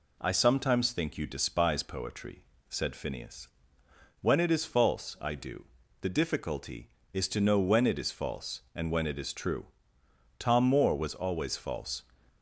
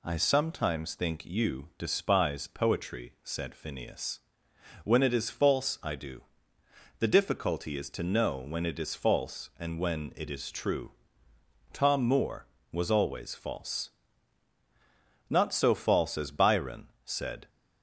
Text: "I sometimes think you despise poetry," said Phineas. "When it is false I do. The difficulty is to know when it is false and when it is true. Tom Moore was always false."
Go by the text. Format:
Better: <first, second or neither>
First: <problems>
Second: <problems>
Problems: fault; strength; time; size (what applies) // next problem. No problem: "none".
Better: first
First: none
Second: goes on to say "Not so false as Byron said"; strong; from 15.2 s on; 2.2 s long